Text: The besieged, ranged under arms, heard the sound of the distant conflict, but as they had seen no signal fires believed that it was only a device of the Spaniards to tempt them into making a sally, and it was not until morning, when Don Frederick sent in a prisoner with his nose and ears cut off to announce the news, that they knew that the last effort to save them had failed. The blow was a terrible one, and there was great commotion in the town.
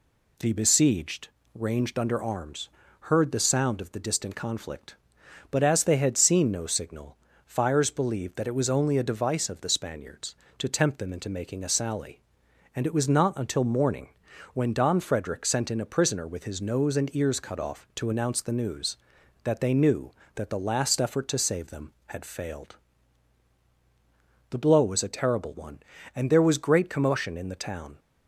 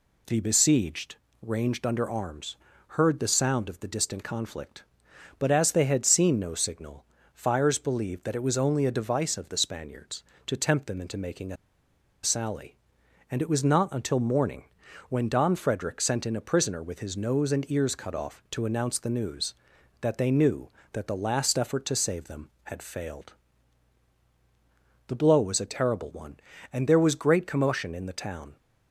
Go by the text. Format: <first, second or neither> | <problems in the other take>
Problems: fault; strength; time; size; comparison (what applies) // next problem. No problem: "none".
first | pauses between "signal" and "fires"; slight; at 7.0 s; 0.30 s long; slight in the first // pauses between "a" and "sally"; noticeable; at 11.5 s; 0.68 s long